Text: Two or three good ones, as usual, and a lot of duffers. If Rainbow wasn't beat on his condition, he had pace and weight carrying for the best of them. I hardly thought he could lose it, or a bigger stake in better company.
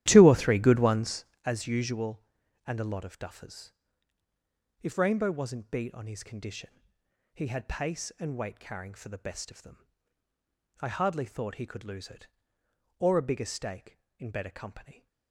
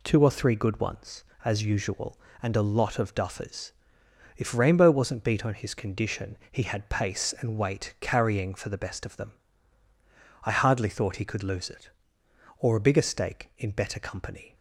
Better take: second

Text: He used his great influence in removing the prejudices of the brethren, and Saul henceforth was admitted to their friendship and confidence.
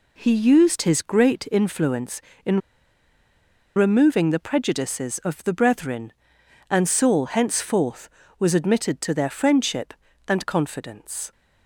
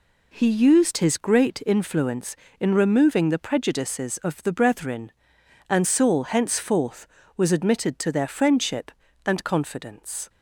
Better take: second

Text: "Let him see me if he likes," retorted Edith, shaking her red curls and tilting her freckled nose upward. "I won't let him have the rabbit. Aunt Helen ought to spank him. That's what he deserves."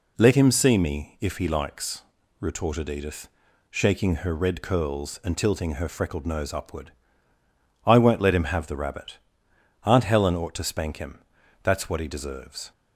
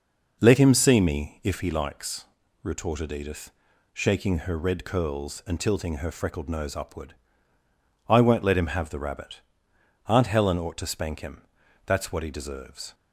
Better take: first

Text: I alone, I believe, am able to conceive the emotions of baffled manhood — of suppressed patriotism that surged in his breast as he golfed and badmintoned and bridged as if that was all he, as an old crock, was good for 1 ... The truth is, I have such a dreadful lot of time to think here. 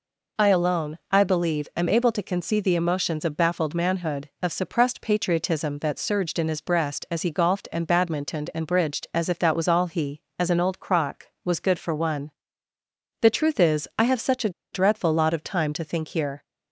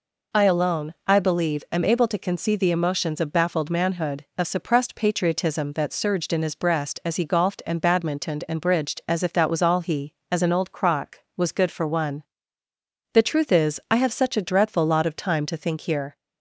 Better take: second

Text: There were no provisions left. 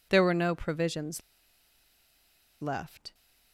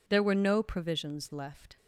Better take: second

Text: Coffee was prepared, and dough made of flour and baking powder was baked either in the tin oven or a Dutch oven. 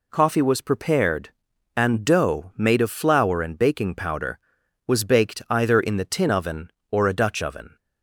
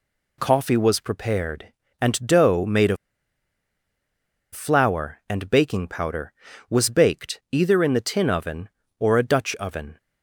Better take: first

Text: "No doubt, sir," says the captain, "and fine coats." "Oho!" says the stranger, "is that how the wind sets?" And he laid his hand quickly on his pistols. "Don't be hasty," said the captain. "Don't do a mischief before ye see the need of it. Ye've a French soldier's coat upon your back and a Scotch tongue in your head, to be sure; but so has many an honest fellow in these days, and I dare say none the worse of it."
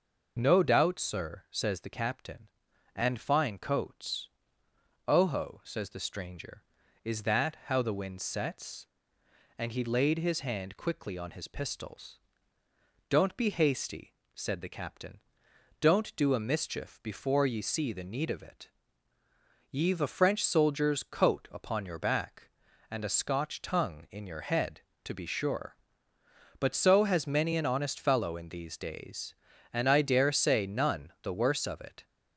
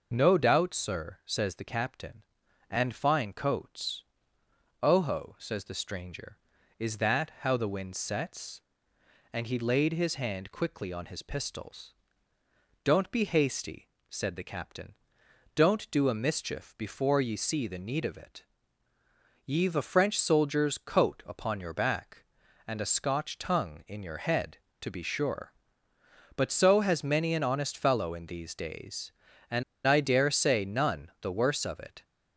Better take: first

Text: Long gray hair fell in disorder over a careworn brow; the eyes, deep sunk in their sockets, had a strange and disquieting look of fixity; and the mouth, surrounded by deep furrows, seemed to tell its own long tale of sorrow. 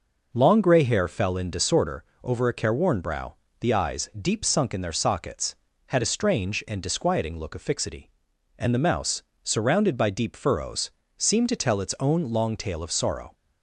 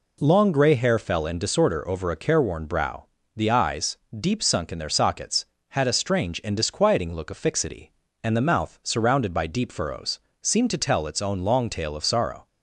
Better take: second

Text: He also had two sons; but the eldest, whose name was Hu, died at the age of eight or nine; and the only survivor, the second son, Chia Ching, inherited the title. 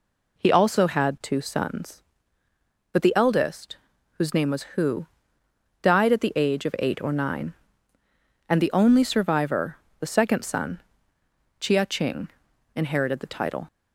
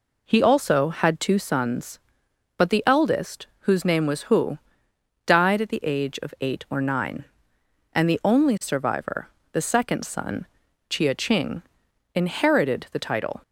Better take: neither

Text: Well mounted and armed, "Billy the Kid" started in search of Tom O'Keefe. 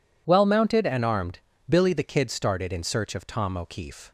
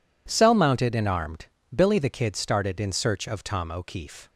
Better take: first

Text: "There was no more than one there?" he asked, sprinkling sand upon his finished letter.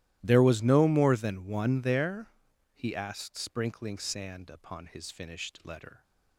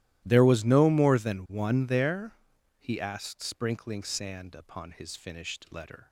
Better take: neither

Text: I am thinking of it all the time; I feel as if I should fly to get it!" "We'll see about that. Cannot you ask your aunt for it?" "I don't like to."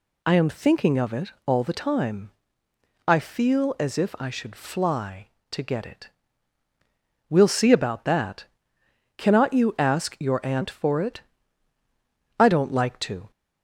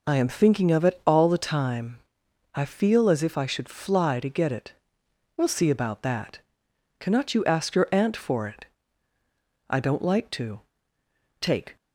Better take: first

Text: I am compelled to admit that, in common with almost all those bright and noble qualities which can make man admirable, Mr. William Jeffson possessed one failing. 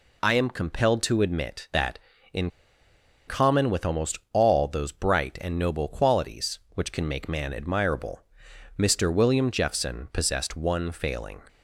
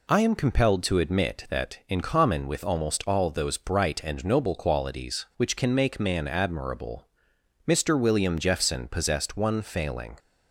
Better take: second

